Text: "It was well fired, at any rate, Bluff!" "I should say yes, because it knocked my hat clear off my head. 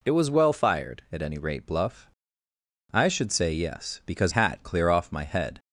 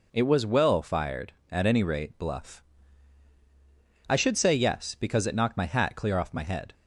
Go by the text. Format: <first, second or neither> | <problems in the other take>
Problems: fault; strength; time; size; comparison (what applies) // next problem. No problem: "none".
second | skips "it knocked my"; at 4.3 s